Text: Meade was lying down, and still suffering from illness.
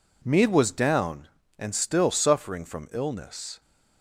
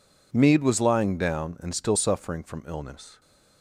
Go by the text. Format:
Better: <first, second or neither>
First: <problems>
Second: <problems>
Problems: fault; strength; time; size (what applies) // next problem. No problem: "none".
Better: second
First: skips "lying"; at 0.7 s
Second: none